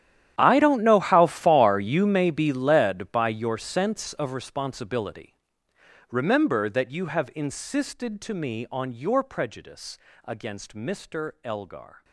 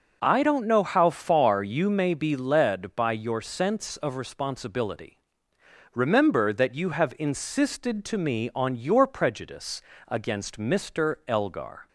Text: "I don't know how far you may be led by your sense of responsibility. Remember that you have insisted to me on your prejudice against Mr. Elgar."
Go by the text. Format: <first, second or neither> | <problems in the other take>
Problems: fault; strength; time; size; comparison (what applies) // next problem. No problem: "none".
second | gets quieter; strong; throughout; 19 dB // pauses between "prejudice" and "against"; slight; at 9.9 s; 0.30 s long; slight in the second